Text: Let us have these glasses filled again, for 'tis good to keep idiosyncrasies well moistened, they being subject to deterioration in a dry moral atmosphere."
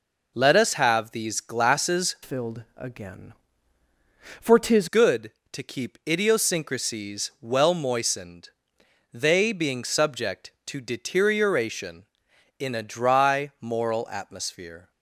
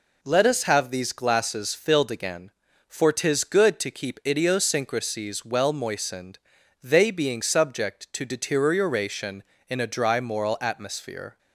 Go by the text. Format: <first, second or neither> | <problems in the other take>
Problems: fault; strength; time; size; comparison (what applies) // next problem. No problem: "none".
second | changes voice from "filled" to "tis"; from 2.2 to 4.8 s; 2.6 s long